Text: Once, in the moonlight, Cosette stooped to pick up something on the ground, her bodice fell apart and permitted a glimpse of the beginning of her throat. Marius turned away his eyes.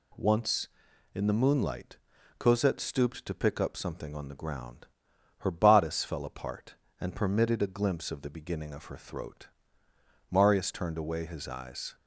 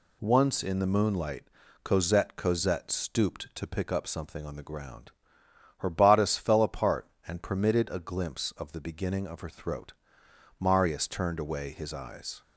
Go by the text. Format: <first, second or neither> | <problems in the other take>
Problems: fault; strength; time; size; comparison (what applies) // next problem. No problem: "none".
first | says "Cosette" twice; at 2.3 s